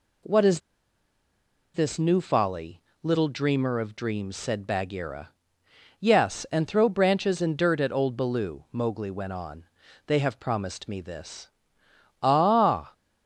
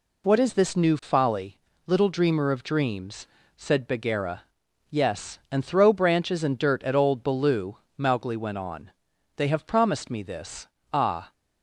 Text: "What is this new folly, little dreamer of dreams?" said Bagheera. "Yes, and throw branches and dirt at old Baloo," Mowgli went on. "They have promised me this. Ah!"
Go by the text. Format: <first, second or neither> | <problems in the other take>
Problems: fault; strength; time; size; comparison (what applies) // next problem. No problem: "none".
second | pauses between "is" and "this"; at 0.6 s; 1.1 s long